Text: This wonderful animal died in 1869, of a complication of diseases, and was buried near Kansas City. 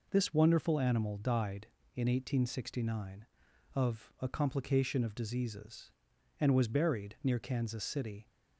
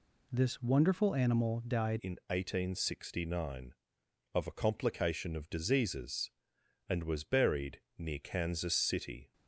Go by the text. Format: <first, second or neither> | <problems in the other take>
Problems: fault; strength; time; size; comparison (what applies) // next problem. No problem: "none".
first | changes voice at "in"; from 1.9 s on; 7.4 s long // pauses between "buried" and "near"; slight; at 7.8 s; 0.18 s long